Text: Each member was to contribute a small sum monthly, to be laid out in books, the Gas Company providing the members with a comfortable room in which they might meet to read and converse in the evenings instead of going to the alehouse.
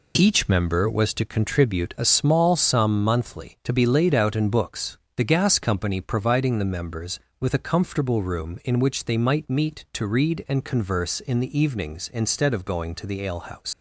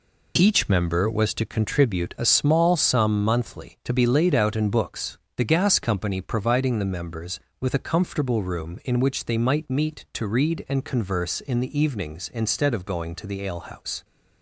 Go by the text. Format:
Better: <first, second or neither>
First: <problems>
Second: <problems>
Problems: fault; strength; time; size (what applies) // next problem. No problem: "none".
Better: second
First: leaves "alehouse" unfinished; at 13.7 s; 110 ms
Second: none